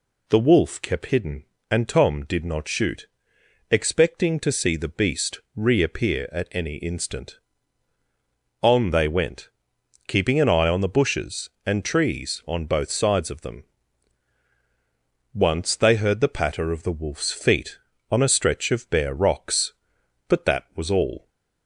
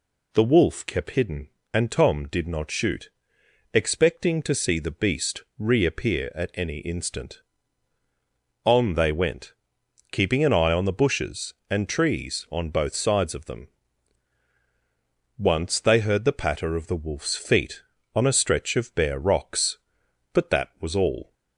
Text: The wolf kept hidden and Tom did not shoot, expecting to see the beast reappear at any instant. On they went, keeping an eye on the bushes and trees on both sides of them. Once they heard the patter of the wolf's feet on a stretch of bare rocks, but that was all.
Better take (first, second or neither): neither